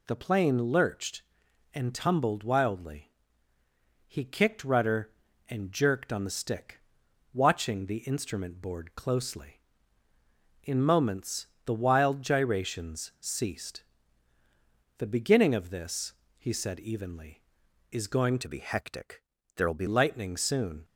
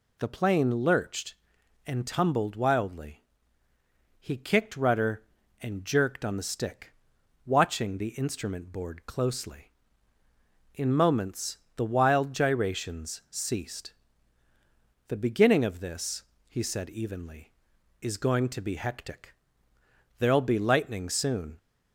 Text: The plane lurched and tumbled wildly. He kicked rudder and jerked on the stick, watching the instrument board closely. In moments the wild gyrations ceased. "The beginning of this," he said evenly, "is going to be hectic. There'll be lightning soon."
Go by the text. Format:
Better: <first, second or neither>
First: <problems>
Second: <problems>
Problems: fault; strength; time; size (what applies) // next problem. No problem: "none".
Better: second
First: pauses between "moments" and "the"; slight; at 11.4 s; 0.18 s long // changes voice from "to" to "be"; from 18.4 to 19.8 s; 1.4 s long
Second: pauses between "moments" and "the"; slight; at 11.5 s; 0.18 s long